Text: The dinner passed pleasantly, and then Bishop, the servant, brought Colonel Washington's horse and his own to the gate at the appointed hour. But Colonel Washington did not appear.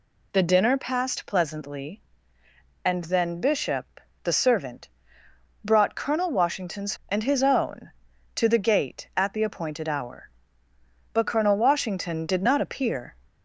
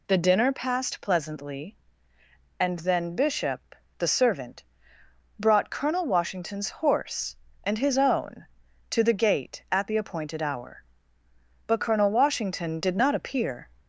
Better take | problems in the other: second | skips "horse"; at 7.0 s

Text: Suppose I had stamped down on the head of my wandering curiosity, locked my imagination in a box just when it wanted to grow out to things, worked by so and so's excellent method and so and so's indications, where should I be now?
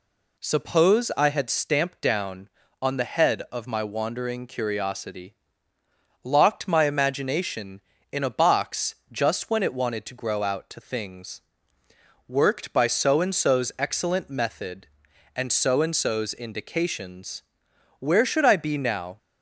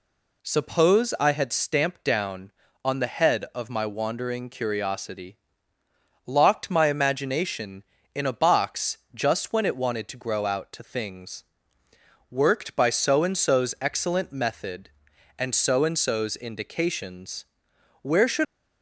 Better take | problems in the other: first | pauses between "box" and "just"; slight; at 8.9 s; 0.16 s long; slight in the first // stops before "I be now"; at 18.4 s

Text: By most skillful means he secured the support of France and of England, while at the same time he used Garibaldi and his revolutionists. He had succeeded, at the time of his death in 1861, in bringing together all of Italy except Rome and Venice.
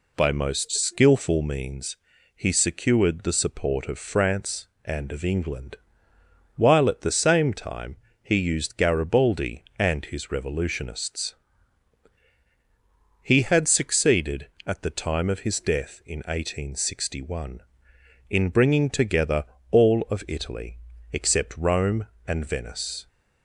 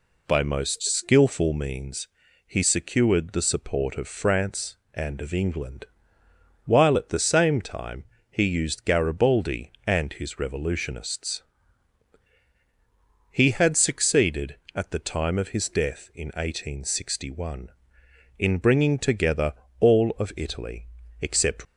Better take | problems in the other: first | pauses between "means" and "he"; at 2.0 s; 0.40 s long; also in the first // pauses between "time" and "he"; slight; at 8.0 s; 0.26 s long; slight in the first // pauses between "together" and "all"; slight; at 19.5 s; 0.26 s long; slight in the first // pauses between "Italy" and "except"; slight; at 20.8 s; 0.34 s long; slight in the first // stops before "Rome and Venice"; at 21.6 s

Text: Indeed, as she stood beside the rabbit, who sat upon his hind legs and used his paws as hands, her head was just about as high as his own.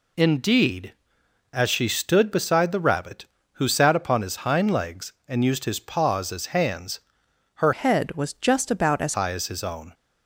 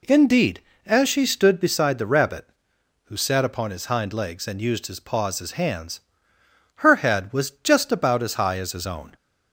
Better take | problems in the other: second | changes voice from "head" to "as"; from 7.7 to 9.1 s; 1.4 s long

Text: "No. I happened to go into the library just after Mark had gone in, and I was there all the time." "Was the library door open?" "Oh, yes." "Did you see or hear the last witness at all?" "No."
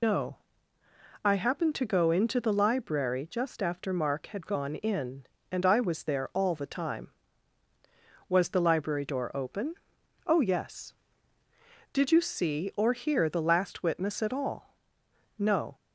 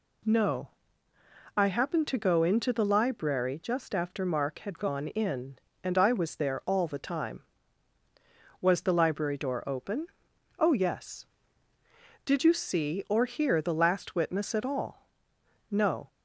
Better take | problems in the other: second | loses the start of "No"; at 0.0 s; 120 ms

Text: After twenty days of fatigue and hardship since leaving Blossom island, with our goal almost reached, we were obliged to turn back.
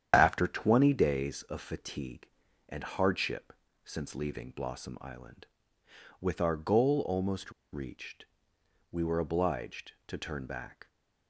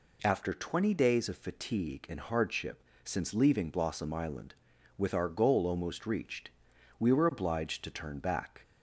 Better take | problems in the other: second | starts louder than the rest; strong; until 1.1 s; 9 dB // pauses between "hardship" and "since"; slight; at 3.5 s; 0.30 s long; slight in the second // pauses between "almost" and "reached"; slight; at 7.5 s; 0.21 s long

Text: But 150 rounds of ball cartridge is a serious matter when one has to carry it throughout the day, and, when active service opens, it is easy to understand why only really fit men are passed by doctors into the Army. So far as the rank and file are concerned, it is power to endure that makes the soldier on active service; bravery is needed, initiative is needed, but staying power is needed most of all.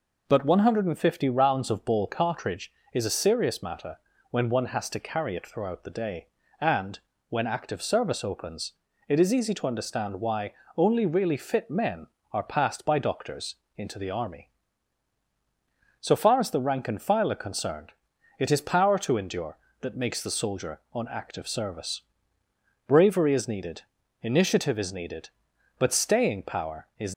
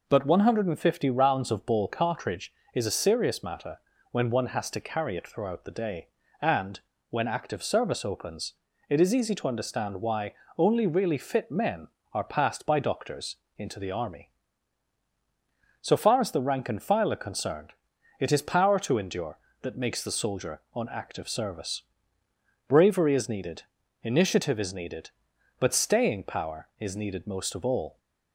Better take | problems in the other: second | pauses between "matter" and "when"; slight; at 3.9 s; 0.34 s long; slight in the second // pauses between "why" and "only"; slight; at 10.5 s; 0.24 s long; slight in the second // pauses between "doctors" and "into"; slight; at 13.5 s; 0.22 s long; slight in the second // stops before "needed most of all"; at 27.1 s

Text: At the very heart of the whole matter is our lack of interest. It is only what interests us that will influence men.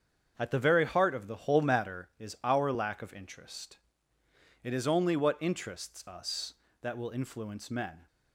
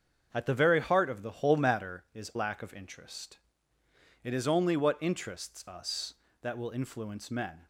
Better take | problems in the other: first | starts louder than the rest; until 1.3 s; 7 dB; strong in the first // skips "our"; at 2.3 s

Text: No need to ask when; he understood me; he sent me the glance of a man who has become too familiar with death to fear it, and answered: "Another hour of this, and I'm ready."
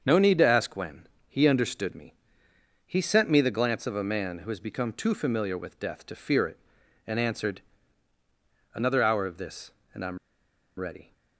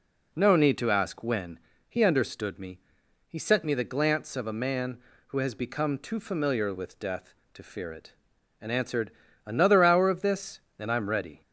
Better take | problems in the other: second | starts louder than the rest; until 1.0 s; 7 dB // pauses between "I'm" and "ready"; noticeable; at 10.1 s; 0.60 s long

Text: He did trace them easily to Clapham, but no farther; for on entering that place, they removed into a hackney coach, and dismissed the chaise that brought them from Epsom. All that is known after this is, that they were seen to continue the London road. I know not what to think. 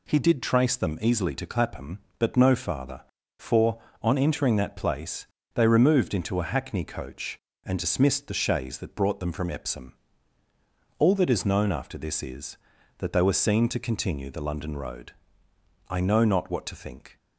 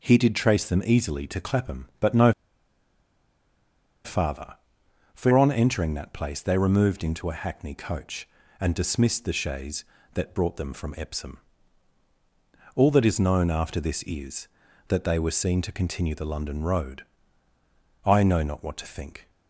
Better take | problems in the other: first | pauses between "no" and "farther"; strong; at 2.3 s; 1.7 s long

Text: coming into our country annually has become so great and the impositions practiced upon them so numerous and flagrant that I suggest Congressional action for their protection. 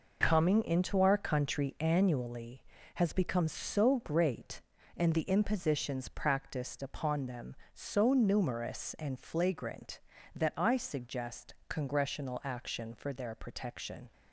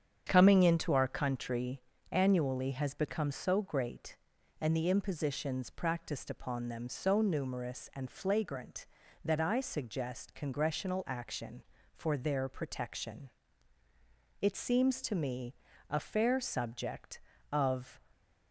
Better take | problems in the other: first | starts louder than the rest; strong; until 1.2 s; 8 dB // pauses between "country" and "annually"; slight; at 1.7 s; 0.32 s long // goes on to say "It seems to me a fair subject of"; strong; from 14.4 s on; 3.5 s long

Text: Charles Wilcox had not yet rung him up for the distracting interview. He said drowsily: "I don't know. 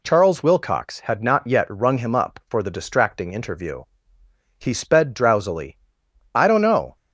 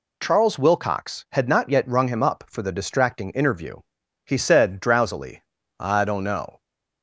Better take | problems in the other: second | says "sped" for "said"; at 4.7 s

